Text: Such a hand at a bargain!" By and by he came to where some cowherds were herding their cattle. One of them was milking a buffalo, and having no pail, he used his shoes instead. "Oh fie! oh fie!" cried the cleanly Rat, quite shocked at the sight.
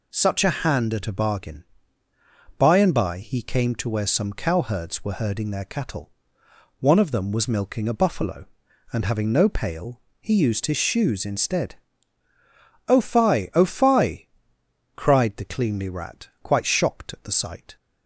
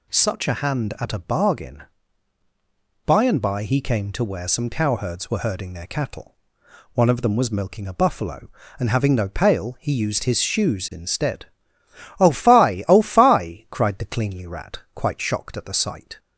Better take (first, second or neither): neither